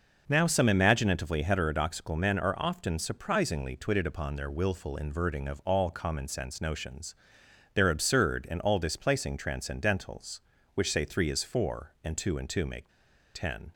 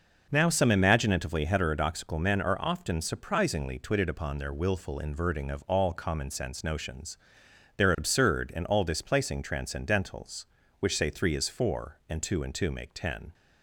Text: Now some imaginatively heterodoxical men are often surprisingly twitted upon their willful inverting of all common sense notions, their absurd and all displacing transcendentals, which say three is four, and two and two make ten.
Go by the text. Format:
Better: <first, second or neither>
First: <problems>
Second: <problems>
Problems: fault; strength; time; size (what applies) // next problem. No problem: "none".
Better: second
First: pauses between "make" and "ten"; at 12.8 s; 0.45 s long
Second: none